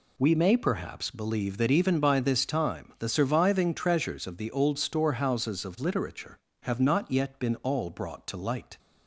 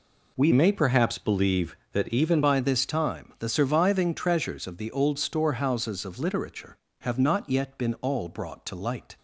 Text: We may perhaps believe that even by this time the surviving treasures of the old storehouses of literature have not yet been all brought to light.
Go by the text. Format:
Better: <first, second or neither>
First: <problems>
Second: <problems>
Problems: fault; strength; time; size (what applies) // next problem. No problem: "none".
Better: first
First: none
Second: changes voice from "may" to "even"; from 0.5 to 2.4 s; 1.9 s long